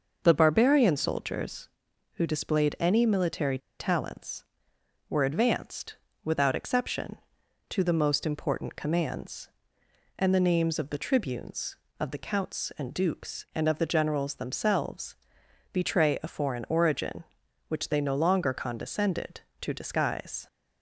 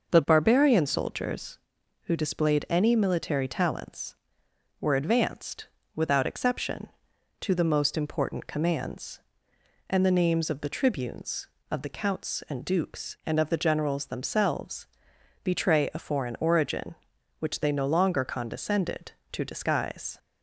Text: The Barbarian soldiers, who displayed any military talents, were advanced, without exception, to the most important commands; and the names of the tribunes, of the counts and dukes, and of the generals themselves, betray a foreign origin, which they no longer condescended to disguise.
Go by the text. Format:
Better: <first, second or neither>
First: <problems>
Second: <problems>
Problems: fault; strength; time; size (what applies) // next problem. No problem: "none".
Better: second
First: starts louder than the rest; noticeable; until 1.2 s; 6 dB // pauses between "military" and "talents"; slight; at 3.5 s; 0.20 s long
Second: starts louder than the rest; noticeable; until 1.1 s; 6 dB